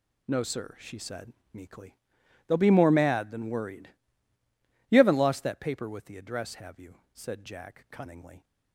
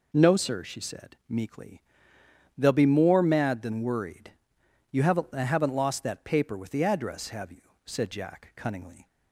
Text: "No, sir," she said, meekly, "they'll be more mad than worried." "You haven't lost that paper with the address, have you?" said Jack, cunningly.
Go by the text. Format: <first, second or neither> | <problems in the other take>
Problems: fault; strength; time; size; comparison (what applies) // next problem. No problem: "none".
first | says "haven't" twice; at 5.3 s